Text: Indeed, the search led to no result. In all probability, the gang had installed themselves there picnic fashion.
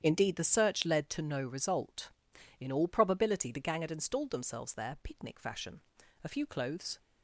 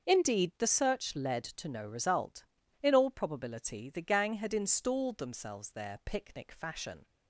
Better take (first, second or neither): second